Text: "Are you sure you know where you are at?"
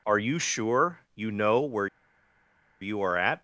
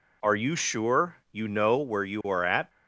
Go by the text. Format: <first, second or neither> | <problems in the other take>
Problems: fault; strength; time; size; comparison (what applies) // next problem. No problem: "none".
second | pauses between "where" and "you"; noticeable; at 1.8 s; 0.93 s long